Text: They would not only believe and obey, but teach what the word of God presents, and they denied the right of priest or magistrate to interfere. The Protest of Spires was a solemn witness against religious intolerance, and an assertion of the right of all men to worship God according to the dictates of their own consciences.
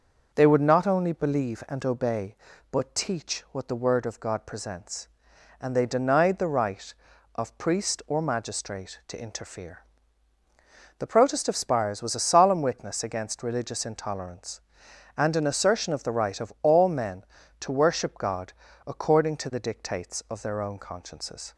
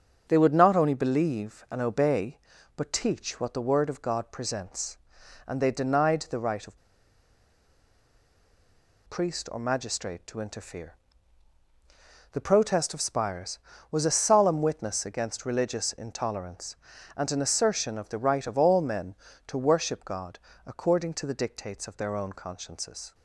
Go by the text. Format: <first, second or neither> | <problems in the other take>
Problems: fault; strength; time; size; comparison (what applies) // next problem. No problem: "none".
first | starts louder than the rest; until 1.2 s; 7 dB; also in the first // pauses between "of" and "priest"; strong; at 6.7 s; 2.3 s long // pauses between "God" and "according"; slight; at 20.3 s; 0.28 s long; slight in the first